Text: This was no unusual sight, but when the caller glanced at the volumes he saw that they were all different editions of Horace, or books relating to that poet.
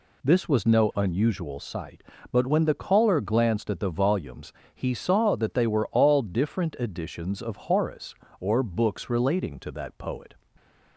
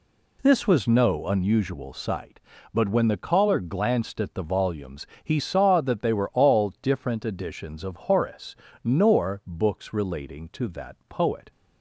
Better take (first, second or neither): first